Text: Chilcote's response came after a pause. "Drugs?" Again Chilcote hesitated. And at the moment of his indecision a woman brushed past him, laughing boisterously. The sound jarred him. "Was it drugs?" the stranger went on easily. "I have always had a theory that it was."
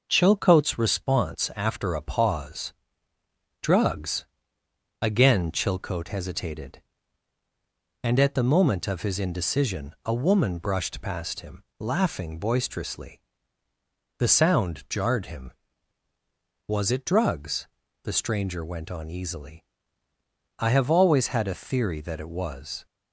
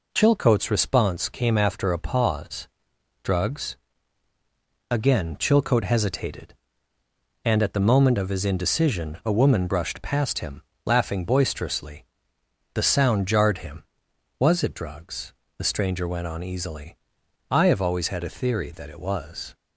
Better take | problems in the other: second | skips "came"; at 1.5 s

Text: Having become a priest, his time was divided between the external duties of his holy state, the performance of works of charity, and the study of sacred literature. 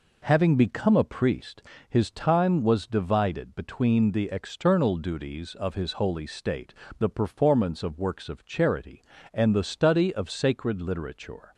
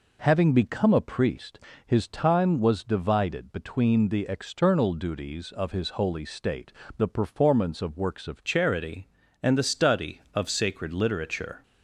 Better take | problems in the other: first | changes voice at "charity"; from 8.4 s on; 3.2 s long

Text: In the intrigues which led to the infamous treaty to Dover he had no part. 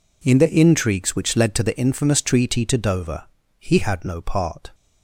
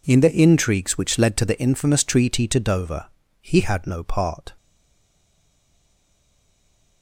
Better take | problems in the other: first | pauses between "Dover" and "he"; slight; at 3.0 s; 0.34 s long; slight in the first // stays silent after the last word; from 4.5 s on; 2.5 s long

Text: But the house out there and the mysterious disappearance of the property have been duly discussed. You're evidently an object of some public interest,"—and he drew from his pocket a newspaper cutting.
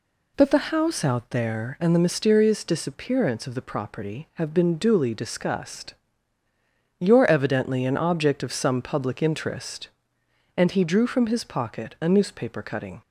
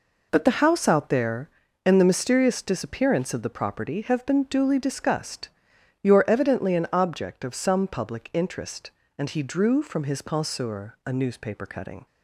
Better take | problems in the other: first | says "penseur" for "pocket"; at 10.2 s

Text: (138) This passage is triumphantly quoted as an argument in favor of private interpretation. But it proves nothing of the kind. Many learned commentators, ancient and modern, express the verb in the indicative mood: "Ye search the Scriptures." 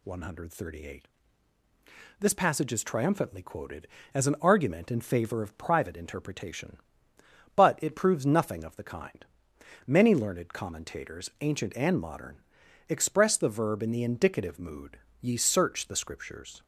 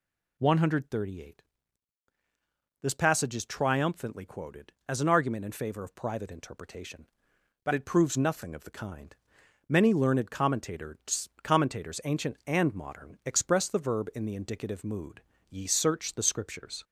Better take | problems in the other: first | says "commentators" twice; at 11.4 s

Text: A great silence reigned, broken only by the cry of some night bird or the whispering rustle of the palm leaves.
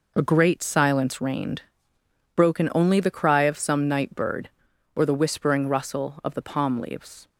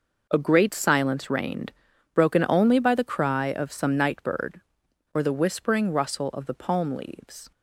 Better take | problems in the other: second | skips "by"; at 3.0 s

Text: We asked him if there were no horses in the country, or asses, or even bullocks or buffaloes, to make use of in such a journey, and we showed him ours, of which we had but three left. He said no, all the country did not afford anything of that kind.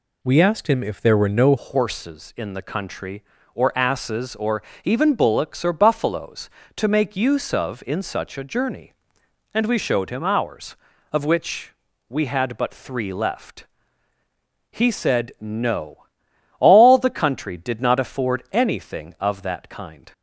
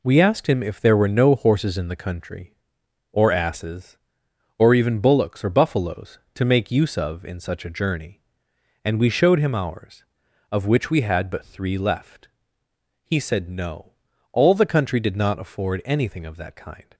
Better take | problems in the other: second | changes voice at "horses"; from 1.5 s on; 18.6 s long // pauses between "or" and "even"; slight; at 4.6 s; 0.22 s long // pauses between "which" and "we"; slight; at 11.7 s; 0.36 s long

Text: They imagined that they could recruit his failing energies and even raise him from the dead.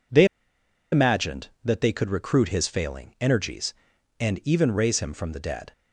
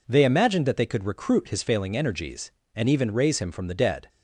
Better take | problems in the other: second | pauses between "They" and "imagined"; noticeable; at 0.2 s; 0.66 s long

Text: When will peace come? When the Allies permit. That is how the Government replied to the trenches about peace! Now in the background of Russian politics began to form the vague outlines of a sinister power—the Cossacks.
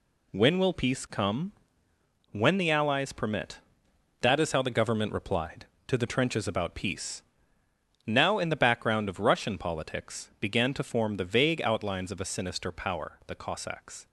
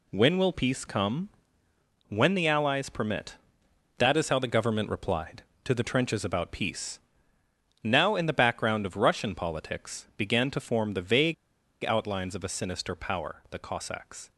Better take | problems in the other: first | pauses between "vague" and "outlines"; noticeable; at 11.3 s; 0.49 s long

